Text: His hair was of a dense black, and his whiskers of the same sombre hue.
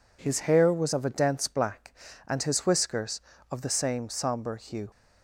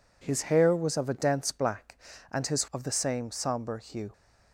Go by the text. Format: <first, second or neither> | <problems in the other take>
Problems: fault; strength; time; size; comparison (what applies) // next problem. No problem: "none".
first | skips "whiskers"; at 2.7 s